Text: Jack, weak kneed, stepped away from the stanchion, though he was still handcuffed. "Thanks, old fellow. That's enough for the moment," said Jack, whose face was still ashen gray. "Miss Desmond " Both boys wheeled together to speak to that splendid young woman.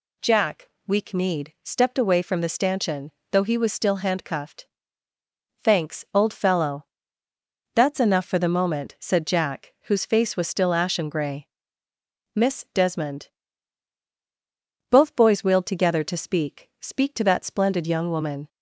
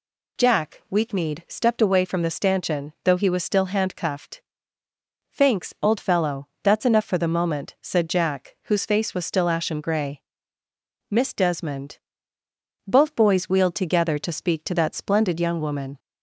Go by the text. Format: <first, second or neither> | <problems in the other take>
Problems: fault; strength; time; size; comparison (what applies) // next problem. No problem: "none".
second | says "speak" twice; at 16.8 s